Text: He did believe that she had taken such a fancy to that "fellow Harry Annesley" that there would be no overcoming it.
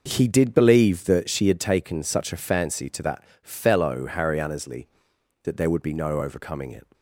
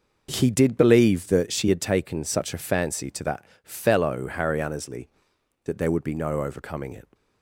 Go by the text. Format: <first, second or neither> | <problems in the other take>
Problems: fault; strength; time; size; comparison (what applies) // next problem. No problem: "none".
neither | pauses between "that" and "fellow"; slight; the same in both